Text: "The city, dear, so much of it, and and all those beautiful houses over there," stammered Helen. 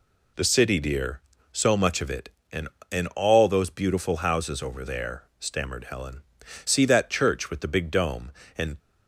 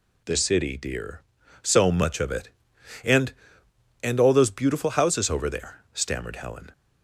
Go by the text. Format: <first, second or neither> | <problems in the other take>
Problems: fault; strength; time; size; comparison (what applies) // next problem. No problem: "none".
second | goes on to say "See that church with the big dome and"; strong; from 6.6 s on; 2.1 s long